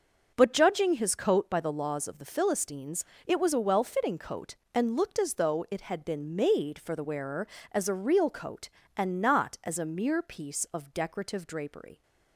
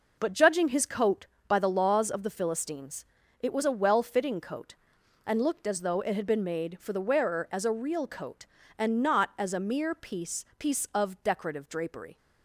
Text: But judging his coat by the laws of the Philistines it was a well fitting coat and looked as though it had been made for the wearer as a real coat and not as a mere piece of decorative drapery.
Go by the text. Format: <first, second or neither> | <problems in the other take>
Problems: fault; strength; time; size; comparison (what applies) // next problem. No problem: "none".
first | pauses between "Philistines" and "it"; slight; at 3.0 s; 0.36 s long; slight in the first // says "piece" twice; at 10.5 s